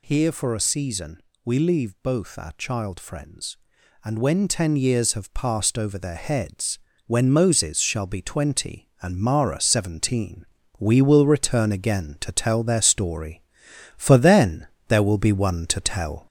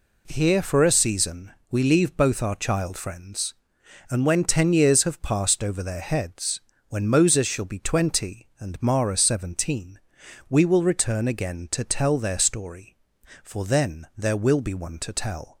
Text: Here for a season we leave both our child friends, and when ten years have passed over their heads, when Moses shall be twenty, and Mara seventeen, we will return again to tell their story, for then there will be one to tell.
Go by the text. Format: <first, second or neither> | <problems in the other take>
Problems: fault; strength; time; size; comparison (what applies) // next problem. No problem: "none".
second | gets louder; slight; throughout; 3 dB // pauses between "season" and "we"; slight; at 1.2 s; 0.24 s long; slight in the second // pauses between "then" and "there"; slight; at 14.6 s; 0.22 s long